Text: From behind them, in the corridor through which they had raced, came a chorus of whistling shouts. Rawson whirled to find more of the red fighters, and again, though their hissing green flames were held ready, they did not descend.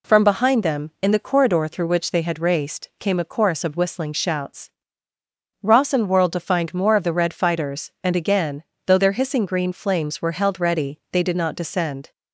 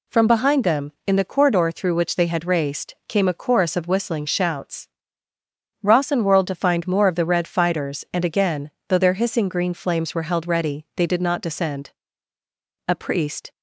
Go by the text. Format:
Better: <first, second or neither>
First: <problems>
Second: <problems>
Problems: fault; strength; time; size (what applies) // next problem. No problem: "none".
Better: first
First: none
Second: goes on to say "A priest"; noticeable; from 12.8 s on; 0.64 s long